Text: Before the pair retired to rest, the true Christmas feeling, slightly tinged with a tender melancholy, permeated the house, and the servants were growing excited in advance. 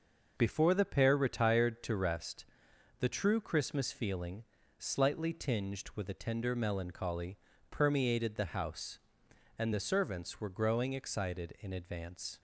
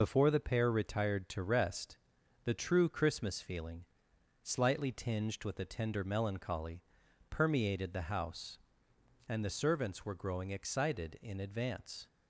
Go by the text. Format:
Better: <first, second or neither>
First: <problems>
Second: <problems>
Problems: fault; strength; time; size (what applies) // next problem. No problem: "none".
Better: first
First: none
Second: loses the start of "Before"; at 0.0 s; 45 ms